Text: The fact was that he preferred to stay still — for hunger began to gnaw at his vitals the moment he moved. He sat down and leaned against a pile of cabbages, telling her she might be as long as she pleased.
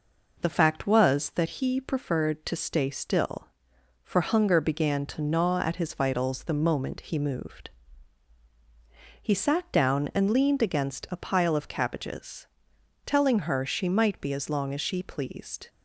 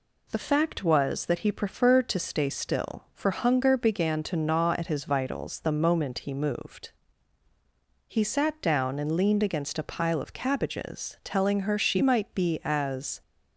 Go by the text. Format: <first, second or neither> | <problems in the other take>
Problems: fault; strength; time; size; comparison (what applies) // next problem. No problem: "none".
first | stops before "long as she pleased"; at 13.2 s